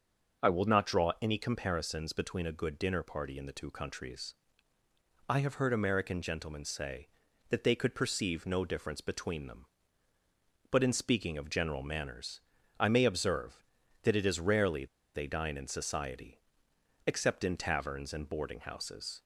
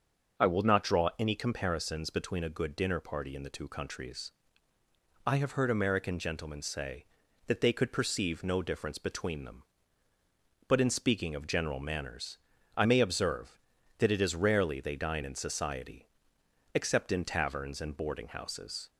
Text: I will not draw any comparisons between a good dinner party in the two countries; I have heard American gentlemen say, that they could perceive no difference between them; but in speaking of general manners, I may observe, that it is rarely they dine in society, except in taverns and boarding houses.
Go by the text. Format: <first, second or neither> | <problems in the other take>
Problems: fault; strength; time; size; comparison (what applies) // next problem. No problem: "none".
second | starts louder than the rest; until 1.5 s; 6 dB; also in the second // pauses between "rarely" and "they"; slight; at 14.8 s; 0.29 s long